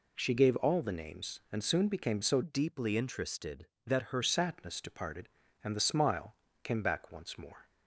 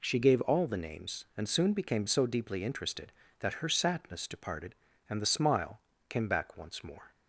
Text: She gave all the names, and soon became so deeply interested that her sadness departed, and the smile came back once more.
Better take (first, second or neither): second